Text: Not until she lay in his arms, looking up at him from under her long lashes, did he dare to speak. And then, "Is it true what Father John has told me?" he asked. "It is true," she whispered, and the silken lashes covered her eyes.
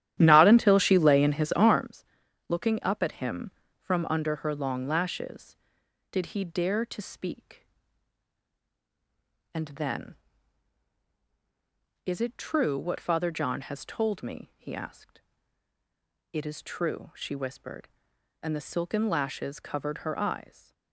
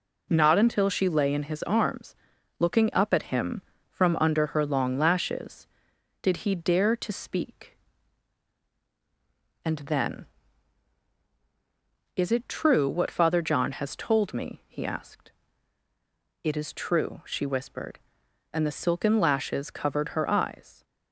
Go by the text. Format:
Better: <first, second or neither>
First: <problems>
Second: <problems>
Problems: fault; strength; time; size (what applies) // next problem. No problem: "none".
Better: second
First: starts louder than the rest; strong; until 1.9 s; 11.5 dB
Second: none